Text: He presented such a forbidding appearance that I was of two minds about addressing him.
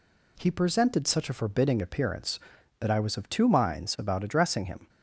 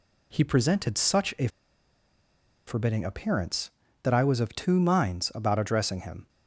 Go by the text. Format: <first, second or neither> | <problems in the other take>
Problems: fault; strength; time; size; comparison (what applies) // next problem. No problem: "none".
first | pauses between "a" and "forbidding"; at 1.4 s; 1.1 s long